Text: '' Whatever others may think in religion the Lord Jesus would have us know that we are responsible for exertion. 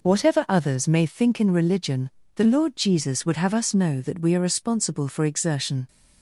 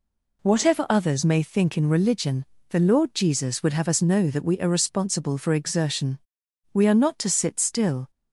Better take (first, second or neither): first